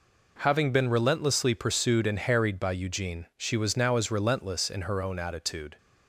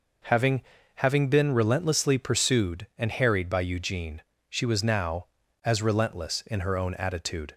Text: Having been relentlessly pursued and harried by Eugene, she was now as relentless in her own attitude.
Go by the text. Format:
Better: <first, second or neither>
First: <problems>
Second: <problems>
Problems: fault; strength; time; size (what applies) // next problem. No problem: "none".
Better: first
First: none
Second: says "Having" twice; at 0.9 s